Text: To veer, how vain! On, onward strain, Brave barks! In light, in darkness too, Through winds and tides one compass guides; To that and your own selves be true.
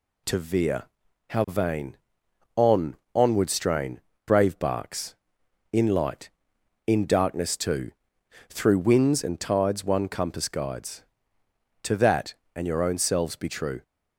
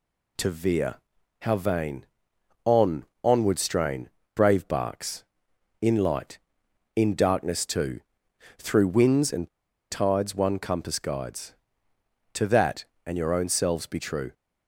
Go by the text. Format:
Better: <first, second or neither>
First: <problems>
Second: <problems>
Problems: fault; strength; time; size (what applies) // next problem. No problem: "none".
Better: first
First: none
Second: pauses between "and" and "tides"; at 9.4 s; 0.43 s long